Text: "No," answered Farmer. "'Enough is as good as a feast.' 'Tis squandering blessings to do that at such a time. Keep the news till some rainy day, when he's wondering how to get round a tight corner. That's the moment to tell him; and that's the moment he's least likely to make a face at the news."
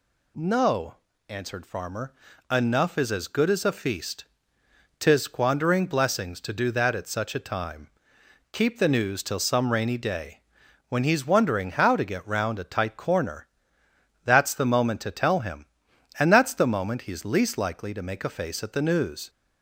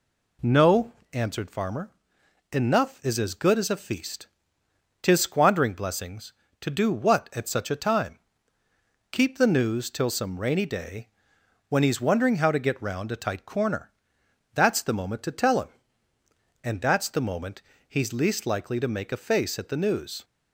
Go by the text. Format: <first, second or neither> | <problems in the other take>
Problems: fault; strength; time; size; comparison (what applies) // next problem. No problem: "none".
first | says "what" for "that"; at 6.9 s // pauses between "moment" and "he's"; slight; at 17.5 s; 0.26 s long